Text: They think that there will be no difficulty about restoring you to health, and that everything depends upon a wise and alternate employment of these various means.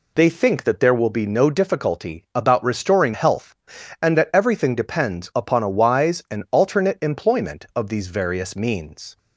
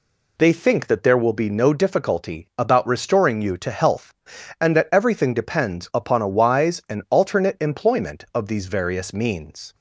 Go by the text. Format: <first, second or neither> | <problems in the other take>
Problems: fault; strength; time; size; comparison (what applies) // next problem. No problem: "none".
second | skips "you to"; at 3.1 s